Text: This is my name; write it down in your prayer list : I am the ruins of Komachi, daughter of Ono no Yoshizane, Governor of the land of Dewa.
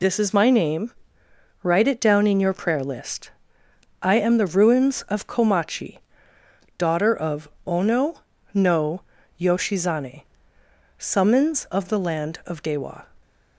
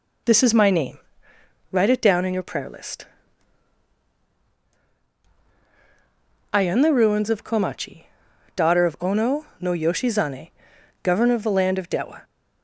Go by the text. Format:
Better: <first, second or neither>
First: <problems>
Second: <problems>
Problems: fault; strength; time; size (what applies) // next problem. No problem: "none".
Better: second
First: pauses between "of" and "Ono"; slight; at 7.4 s; 0.20 s long // pauses between "Ono" and "no"; slight; at 8.1 s; 0.36 s long // pauses between "no" and "Yoshizane"; at 9.0 s; 0.38 s long // says "Summons" for "Governor"; at 10.9 s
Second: none